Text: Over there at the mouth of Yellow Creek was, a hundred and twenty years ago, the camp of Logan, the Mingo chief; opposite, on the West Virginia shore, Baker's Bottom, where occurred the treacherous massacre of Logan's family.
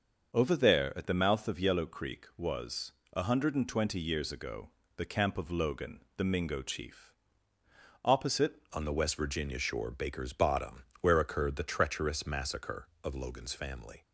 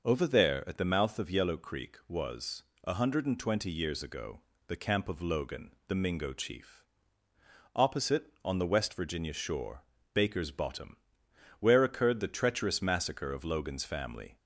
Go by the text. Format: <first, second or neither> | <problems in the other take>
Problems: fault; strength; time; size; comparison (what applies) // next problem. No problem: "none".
second | starts louder than the rest; until 1.3 s; 6.5 dB // changes voice at "on"; from 8.7 s on; 5.3 s long